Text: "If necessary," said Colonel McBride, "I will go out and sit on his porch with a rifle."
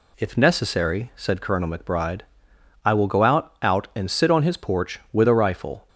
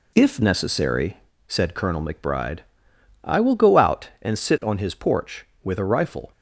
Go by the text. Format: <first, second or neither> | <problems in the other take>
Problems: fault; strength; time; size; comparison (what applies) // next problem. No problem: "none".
second | says "out" twice; at 3.6 s